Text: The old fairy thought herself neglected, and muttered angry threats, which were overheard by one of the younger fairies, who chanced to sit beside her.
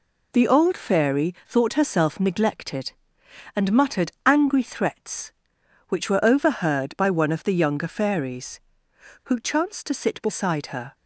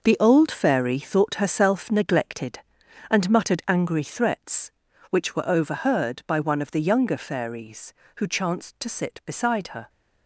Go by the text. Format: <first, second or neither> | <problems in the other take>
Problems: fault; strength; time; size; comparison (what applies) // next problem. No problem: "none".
first | gets quieter; strong; throughout; 10 dB